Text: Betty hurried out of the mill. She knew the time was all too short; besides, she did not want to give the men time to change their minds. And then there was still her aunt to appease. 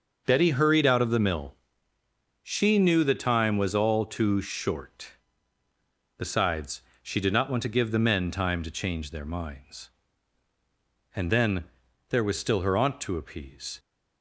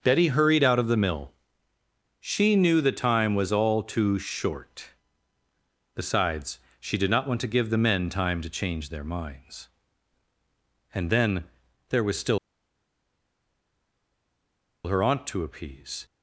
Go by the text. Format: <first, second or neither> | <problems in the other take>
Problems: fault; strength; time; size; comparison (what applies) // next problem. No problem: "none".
first | starts louder than the rest; until 1.0 s; 6 dB; also in the first // pauses between "then" and "there"; at 11.4 s; 0.44 s long; also in the first // pauses between "still" and "her"; strong; at 12.3 s; 2.4 s long